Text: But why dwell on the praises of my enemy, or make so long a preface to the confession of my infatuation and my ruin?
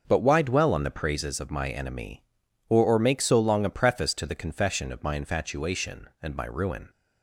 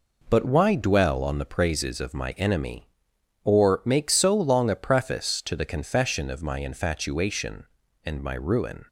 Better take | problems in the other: second | starts louder than the rest; until 1.0 s; 6.5 dB // says "or" twice; at 2.8 s

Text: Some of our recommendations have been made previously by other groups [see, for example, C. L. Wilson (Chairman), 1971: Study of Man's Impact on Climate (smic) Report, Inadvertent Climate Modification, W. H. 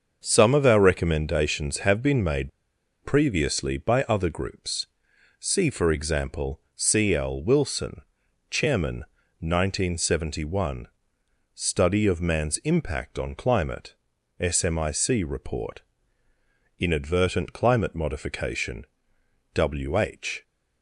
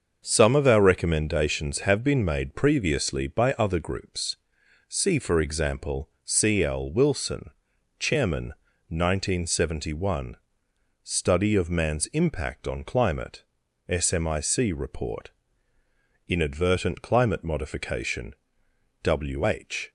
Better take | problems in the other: second | starts louder than the rest; until 1.2 s; 6.5 dB; also in the second // pauses between "made" and "previously"; noticeable; at 2.5 s; 0.53 s long // pauses between "groups" and "see"; noticeable; at 4.8 s; 0.52 s long; noticeable in the second

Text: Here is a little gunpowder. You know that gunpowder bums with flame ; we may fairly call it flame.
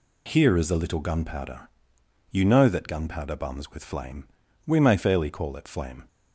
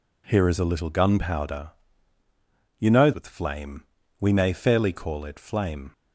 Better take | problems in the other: first | skips "that gunpowder bums"; at 3.1 s

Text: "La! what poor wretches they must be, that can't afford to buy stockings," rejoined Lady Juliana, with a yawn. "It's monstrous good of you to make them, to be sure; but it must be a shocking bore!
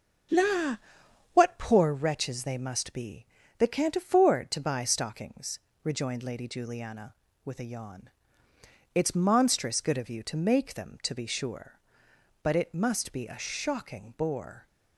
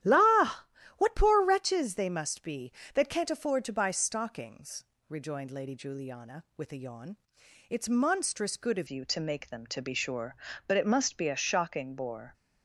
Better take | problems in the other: first | starts louder than the rest; strong; until 1.3 s; 12 dB; also in the first // changes voice at "you"; from 8.8 s on; 3.5 s long

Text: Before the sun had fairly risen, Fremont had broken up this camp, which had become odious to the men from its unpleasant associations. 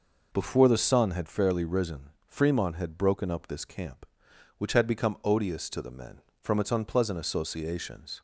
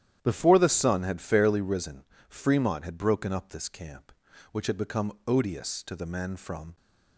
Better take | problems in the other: first | starts louder than the rest; strong; until 1.2 s; 10.5 dB // stops before "its unpleasant associations"; at 6.7 s

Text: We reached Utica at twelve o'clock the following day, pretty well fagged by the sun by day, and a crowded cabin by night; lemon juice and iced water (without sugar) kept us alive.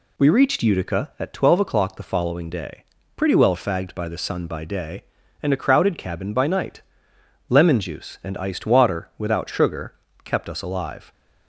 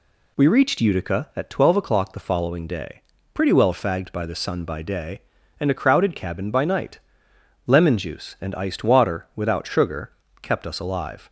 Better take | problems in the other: neither | none

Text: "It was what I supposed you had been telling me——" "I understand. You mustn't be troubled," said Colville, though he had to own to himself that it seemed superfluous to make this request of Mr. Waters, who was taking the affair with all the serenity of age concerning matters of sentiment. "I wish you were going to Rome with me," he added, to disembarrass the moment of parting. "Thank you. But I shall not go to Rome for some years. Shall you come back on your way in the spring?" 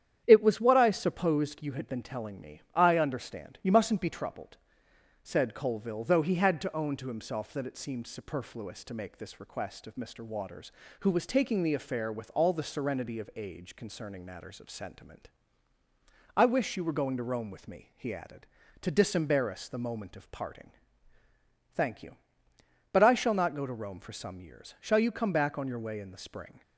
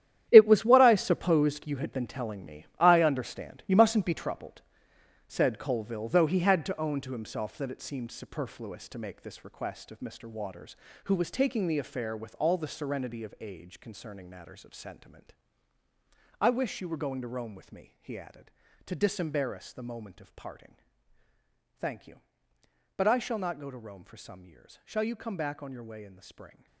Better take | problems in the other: first | gets quieter; strong; throughout; 12 dB // starts louder than the rest; strong; until 1.3 s; 10.5 dB; strong in the first

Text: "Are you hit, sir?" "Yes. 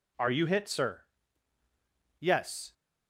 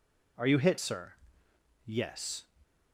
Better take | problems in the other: neither | none

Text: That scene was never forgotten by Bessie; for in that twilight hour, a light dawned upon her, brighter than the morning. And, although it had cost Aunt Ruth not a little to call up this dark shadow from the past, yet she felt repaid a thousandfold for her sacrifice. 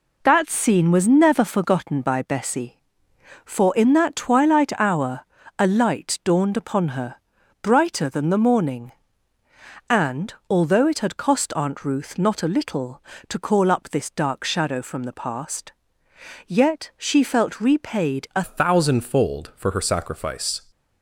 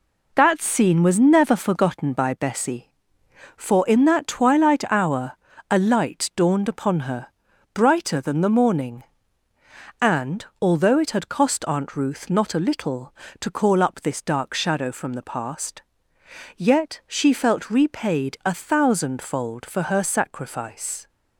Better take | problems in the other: second | changes voice at "thousandfold"; from 18.4 s on; 2.2 s long

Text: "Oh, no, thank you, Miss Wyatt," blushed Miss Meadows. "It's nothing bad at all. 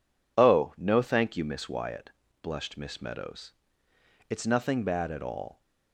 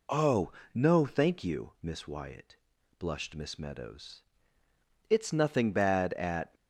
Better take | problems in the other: first | stops before "all"; at 6.5 s

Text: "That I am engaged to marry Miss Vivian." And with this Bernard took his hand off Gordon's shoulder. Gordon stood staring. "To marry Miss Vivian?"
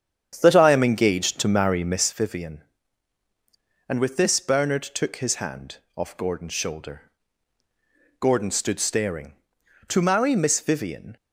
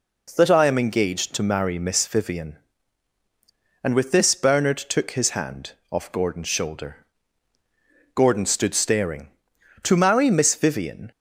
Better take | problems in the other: second | starts louder than the rest; strong; until 2.2 s; 8.5 dB // pauses between "hand" and "off"; slight; at 5.7 s; 0.18 s long; slight in the second

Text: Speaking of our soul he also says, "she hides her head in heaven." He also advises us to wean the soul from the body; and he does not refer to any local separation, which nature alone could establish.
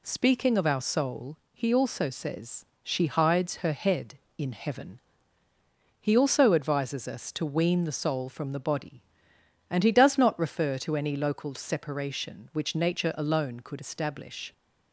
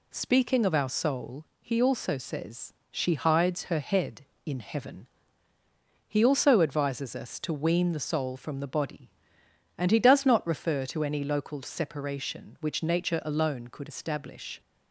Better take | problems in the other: neither | pauses between "soul" and "he"; slight; the same in both

